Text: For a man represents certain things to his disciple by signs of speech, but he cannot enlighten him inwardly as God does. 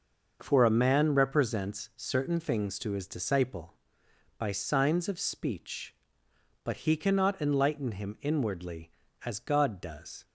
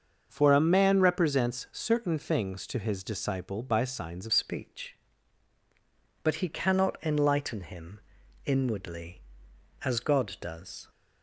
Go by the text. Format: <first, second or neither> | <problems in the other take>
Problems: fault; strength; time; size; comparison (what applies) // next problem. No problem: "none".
first | starts louder than the rest; until 1.3 s; 6.5 dB; noticeable in the first // changes voice at "speech"; from 4.3 s on; 6.5 s long // pauses between "him" and "inwardly"; at 8.0 s; 0.44 s long